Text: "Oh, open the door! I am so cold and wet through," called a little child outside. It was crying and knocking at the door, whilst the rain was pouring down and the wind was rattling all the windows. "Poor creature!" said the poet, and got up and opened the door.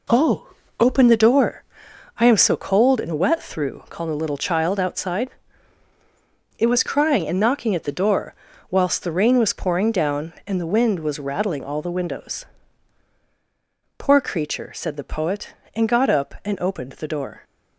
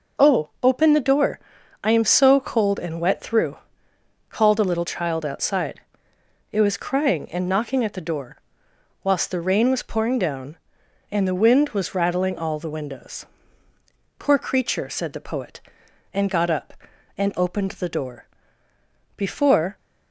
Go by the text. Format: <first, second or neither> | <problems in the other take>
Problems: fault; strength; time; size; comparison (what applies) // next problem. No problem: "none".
first | goes on to say "Before"; from 19.1 s on; 0.60 s long